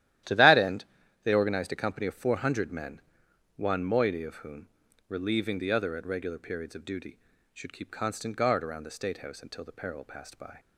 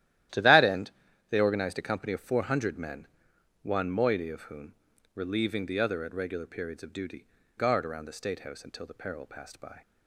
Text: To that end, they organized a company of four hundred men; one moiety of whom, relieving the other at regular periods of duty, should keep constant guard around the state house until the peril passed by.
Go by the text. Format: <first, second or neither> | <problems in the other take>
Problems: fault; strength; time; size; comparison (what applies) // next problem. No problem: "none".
first | starts louder than the rest; strong; until 1.7 s; 13 dB; strong in the first // skips "should keep constant"; at 7.4 s